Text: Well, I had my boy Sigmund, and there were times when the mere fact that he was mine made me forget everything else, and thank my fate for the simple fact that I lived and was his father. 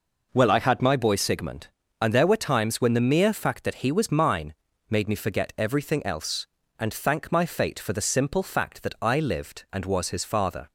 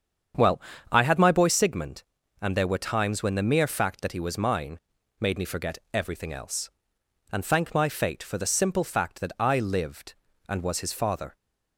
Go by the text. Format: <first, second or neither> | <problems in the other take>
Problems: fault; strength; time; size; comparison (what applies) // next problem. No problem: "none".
first | starts louder than the rest; strong; until 1.6 s; 8 dB // pauses between "mine" and "made"; at 4.7 s; 0.40 s long; slight in the first // pauses between "forget" and "everything"; slight; at 5.7 s; 0.16 s long